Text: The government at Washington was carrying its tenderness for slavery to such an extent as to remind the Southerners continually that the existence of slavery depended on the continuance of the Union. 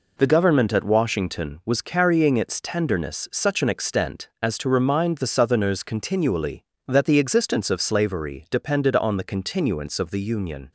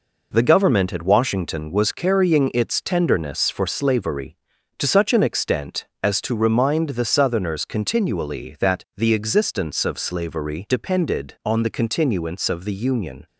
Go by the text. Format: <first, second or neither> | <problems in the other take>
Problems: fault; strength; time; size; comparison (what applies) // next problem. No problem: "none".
second | skips "for slavery to"; at 3.2 s